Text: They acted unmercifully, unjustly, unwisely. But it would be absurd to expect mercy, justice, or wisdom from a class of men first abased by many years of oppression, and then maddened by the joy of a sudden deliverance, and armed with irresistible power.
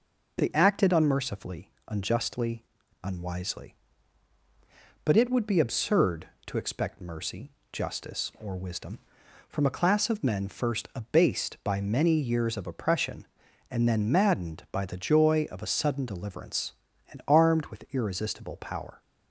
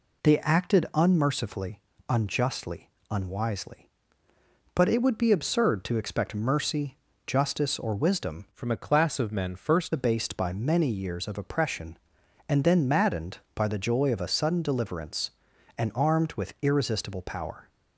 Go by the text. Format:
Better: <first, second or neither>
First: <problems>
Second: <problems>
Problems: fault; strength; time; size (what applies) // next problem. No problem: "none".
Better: first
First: none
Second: changes voice from "from" to "first"; from 8.5 to 9.9 s; 1.4 s long